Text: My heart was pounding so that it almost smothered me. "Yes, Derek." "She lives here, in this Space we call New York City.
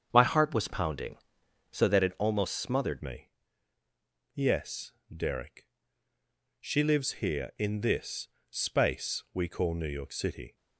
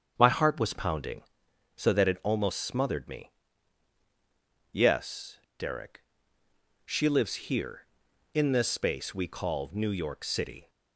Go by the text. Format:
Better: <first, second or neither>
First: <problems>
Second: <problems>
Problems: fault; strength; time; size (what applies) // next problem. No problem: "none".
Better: second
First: starts louder than the rest; strong; until 1.1 s; 7.5 dB // changes voice at "me"; from 3.0 s on; 7.5 s long // pauses between "this" and "Space"; slight; at 8.2 s; 0.24 s long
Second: starts louder than the rest; strong; until 1.1 s; 7.5 dB